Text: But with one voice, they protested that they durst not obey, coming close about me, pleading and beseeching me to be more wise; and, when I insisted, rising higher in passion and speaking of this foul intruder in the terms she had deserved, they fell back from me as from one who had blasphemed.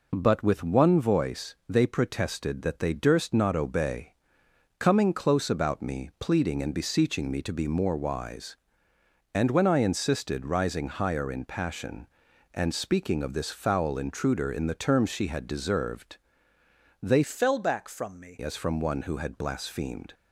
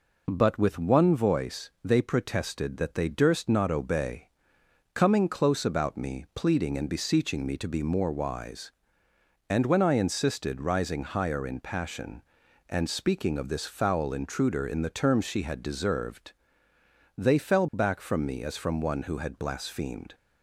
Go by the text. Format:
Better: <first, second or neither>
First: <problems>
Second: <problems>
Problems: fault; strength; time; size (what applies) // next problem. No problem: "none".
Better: second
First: changes voice from "fell" to "me"; from 17.2 to 18.3 s; 1.1 s long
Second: none